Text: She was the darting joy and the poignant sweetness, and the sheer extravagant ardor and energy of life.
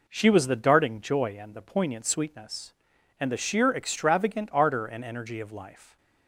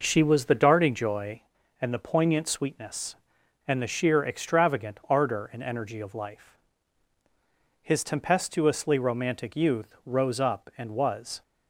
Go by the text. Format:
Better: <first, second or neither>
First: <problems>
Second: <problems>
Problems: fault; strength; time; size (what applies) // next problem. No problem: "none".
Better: first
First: none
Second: goes on to say "His tempestuously romantic youth rose up and was"; strong; from 7.8 s on; 3.5 s long